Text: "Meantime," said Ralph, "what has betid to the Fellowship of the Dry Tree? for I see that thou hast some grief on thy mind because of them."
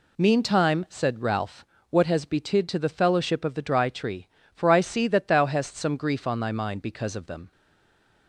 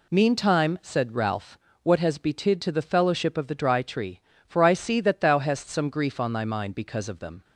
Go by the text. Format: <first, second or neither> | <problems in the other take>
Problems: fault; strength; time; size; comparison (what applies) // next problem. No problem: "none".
second | stays silent after the last word; slight; from 7.5 s on; 0.7 s long